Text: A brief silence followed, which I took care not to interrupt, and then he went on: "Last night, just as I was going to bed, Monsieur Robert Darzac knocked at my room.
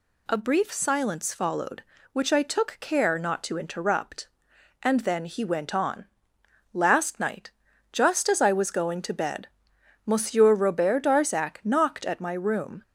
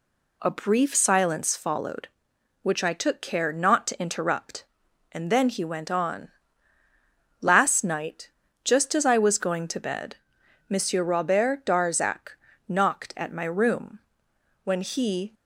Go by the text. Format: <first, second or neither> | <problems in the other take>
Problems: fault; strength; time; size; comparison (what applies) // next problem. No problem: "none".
first | pauses between "Darzac" and "knocked"; slight; at 12.3 s; 0.32 s long // goes on to say "When he"; noticeable; from 14.6 s on; 0.70 s long